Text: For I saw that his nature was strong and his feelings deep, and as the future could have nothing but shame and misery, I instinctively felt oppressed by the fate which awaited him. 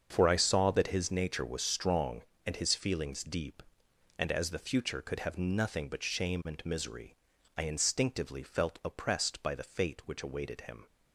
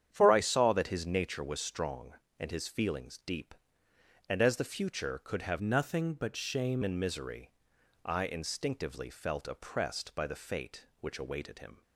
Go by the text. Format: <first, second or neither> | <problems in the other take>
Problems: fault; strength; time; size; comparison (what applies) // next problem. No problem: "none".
first | starts louder than the rest; strong; until 1.1 s; 9 dB; also in the first // changes voice from "nothing" to "shame"; from 5.6 to 6.8 s; 1.2 s long